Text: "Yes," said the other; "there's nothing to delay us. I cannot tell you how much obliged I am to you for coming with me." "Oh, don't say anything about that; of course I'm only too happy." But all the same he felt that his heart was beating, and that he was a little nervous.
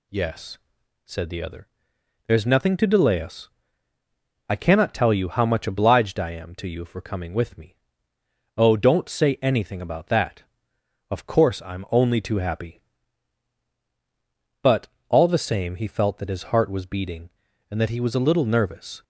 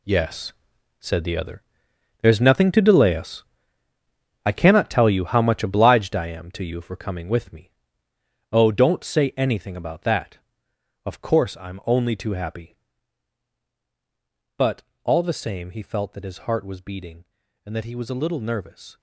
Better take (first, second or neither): first